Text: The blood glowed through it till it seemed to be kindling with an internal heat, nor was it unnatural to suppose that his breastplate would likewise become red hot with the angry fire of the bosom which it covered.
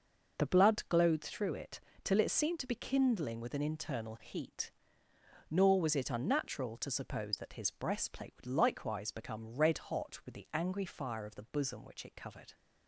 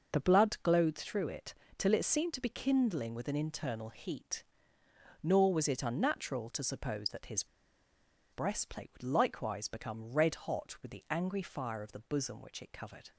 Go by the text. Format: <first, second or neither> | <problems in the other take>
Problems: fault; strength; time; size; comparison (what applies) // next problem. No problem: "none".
first | starts louder than the rest; noticeable; until 1.1 s; 6 dB; noticeable in the first // pauses between "it" and "till"; slight; at 1.5 s; 0.24 s long; slight in the first // pauses between "his" and "breastplate"; noticeable; at 7.4 s; 0.87 s long